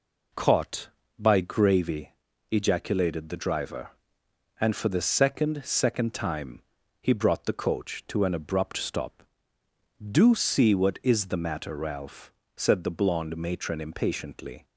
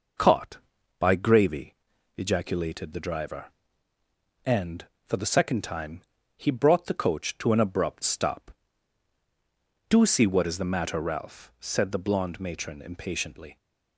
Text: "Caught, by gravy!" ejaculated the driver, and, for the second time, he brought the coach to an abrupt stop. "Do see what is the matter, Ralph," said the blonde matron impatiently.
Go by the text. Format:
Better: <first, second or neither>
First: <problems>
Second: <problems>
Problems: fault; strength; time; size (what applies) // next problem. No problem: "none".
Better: second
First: says "second" twice; at 5.6 s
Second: none